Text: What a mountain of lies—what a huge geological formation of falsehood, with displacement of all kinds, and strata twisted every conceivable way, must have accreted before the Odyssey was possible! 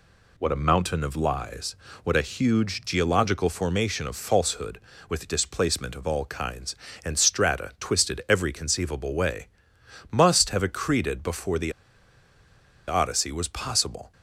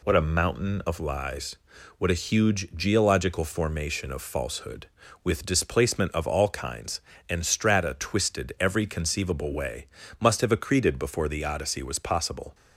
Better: second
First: pauses between "the" and "Odyssey"; at 11.7 s; 1.1 s long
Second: none

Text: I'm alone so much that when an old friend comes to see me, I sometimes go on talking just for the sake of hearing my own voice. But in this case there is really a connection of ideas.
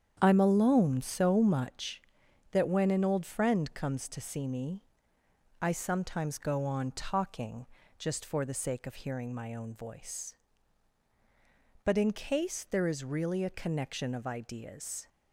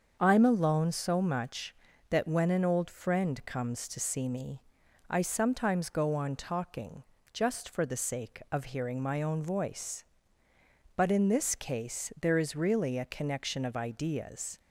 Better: second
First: starts louder than the rest; strong; until 1.2 s; 8.5 dB // pauses between "talking" and "just"; slight; at 7.6 s; 0.34 s long // skips "this"; at 12.1 s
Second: starts louder than the rest; until 1.2 s; 6.5 dB // pauses between "talking" and "just"; slight; at 7.0 s; 0.30 s long

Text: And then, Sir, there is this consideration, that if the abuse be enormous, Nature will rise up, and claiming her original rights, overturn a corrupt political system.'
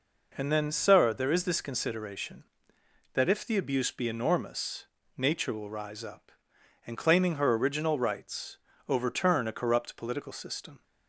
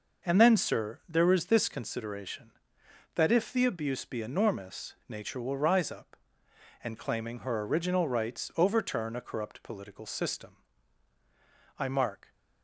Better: first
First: none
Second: goes on to say "I mark"; from 11.7 s on; 0.54 s long

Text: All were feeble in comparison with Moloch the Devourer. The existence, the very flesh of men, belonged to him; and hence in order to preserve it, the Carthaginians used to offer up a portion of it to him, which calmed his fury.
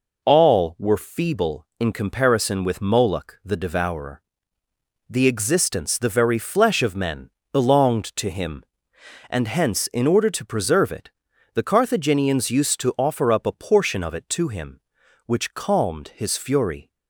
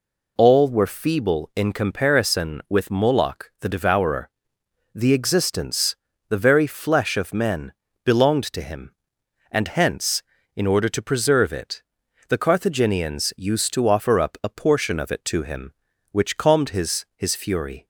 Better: first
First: none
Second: says "his" twice; at 17.1 s

